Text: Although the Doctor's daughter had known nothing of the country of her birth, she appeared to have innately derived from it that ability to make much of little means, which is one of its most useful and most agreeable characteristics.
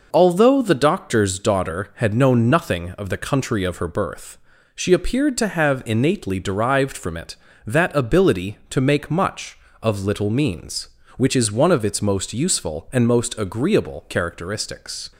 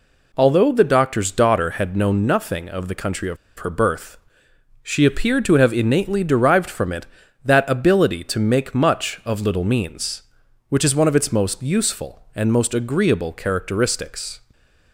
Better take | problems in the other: first | pauses between "of" and "her"; slight; at 3.3 s; 0.22 s long // stays silent after the last word; slight; from 14.4 s on; 0.5 s long

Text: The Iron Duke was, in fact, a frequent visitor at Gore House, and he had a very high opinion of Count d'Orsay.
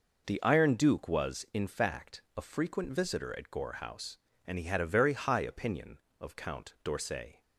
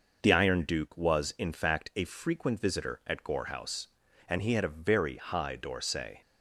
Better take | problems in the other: first | skips "opinion of Count"; at 5.5 s

